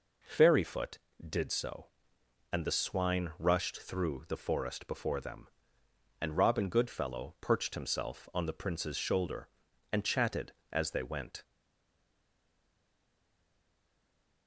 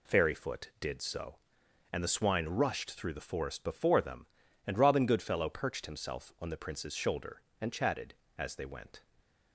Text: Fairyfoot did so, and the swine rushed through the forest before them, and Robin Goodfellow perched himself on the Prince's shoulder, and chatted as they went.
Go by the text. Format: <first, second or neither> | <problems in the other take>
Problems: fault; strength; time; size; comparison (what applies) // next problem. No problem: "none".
second | stays silent after the last word; strong; from 11.4 s on; 3.0 s long